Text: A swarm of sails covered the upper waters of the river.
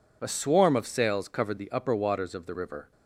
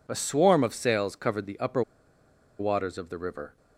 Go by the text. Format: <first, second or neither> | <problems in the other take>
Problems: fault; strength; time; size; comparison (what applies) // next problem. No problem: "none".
first | pauses between "upper" and "waters"; noticeable; at 1.8 s; 0.78 s long